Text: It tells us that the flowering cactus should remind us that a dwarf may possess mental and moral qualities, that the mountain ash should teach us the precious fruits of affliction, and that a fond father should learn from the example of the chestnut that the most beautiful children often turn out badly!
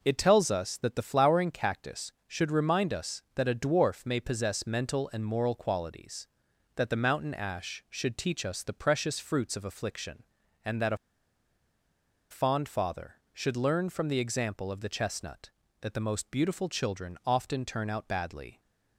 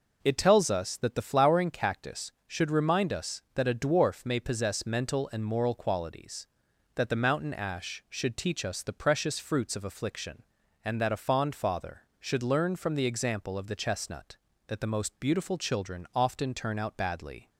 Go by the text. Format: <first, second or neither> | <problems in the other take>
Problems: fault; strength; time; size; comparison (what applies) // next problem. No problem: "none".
second | pauses between "a" and "fond"; strong; at 10.9 s; 1.3 s long